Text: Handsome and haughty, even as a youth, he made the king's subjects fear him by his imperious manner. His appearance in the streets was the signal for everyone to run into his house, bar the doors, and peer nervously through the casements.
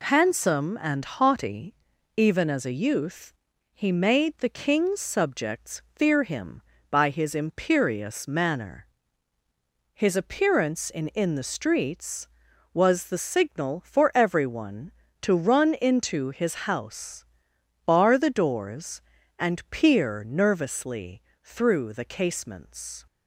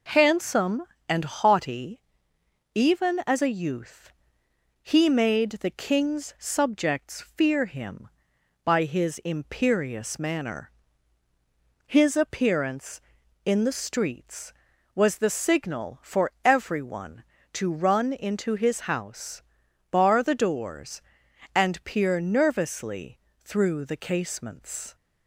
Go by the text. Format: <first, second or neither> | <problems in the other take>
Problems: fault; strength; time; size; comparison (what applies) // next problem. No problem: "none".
second | says "in" twice; at 11.0 s // pauses between "nervously" and "through"; slight; at 21.2 s; 0.22 s long; slight in the second